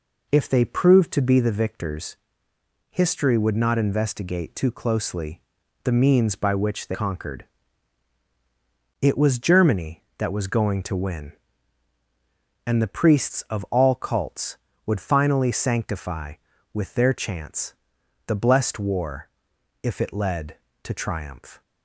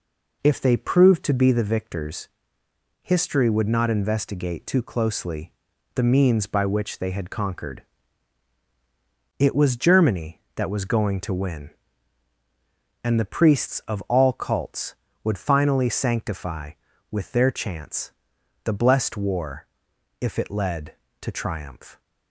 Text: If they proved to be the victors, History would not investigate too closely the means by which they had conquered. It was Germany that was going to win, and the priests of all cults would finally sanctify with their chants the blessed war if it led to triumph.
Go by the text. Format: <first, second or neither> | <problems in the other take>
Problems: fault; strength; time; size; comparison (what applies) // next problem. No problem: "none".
second | pauses between "closely" and "the"; at 5.3 s; 0.44 s long; also in the second // skips "had"; at 6.9 s // pauses between "chants" and "the"; noticeable; at 17.7 s; 0.54 s long; noticeable in the second // pauses between "war" and "if"; noticeable; at 19.2 s; 0.56 s long; noticeable in the second